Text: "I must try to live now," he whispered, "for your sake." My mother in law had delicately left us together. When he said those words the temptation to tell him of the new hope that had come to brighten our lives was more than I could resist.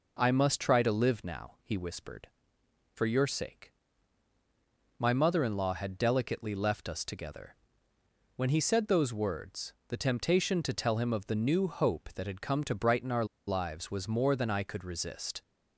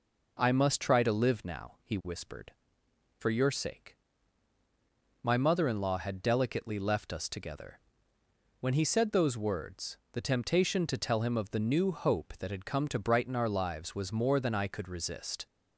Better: second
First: pauses between "words" and "the"; slight; at 9.7 s; 0.16 s long // pauses between "our" and "lives"; slight; at 13.2 s; 0.21 s long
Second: pauses between "words" and "the"; slight; at 9.9 s; 0.16 s long

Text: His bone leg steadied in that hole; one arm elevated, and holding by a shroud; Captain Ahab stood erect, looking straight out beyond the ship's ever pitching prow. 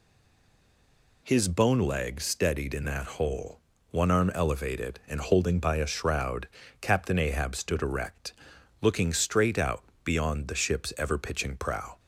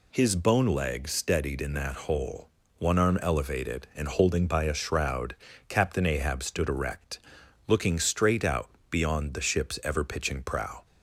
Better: second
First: stays silent before the first word; noticeable; until 1.2 s; 1.2 s long // pauses between "out" and "beyond"; slight; at 9.8 s; 0.20 s long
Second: pauses between "out" and "beyond"; slight; at 8.6 s; 0.20 s long

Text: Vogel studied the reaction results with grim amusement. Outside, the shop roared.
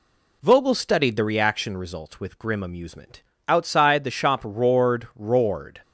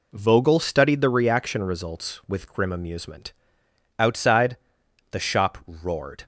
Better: second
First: says "roared" twice; at 5.1 s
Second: none

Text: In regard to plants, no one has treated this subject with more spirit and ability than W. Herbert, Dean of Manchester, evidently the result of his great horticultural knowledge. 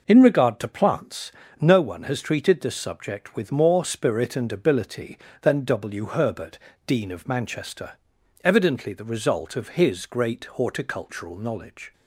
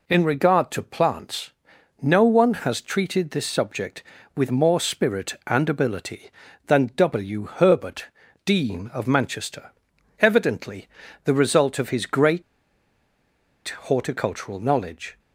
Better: first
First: none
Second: pauses between "evidently" and "the"; at 10.8 s; 0.38 s long // pauses between "great" and "horticultural"; strong; at 12.4 s; 1.4 s long

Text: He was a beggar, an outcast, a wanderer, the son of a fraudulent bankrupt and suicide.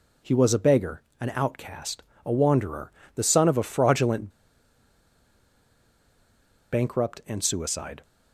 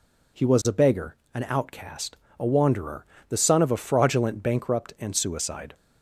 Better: second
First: pauses between "fraudulent" and "bankrupt"; strong; at 4.2 s; 2.4 s long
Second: none

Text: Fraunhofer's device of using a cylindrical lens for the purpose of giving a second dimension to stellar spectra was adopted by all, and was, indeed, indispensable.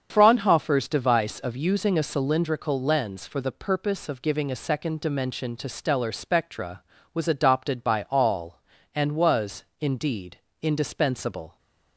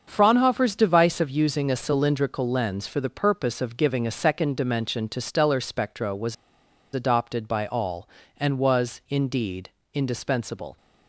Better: first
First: starts louder than the rest; strong; until 1.1 s; 7 dB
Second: starts louder than the rest; until 1.0 s; 6.5 dB // pauses between "was" and "adopted"; noticeable; at 6.3 s; 0.58 s long

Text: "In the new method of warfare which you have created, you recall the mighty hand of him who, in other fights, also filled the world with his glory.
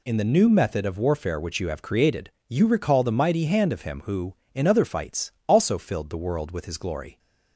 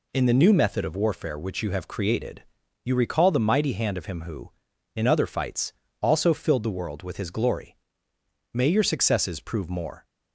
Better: first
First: none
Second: goes on to say "May your successes prove more"; from 8.5 s on; 1.5 s long

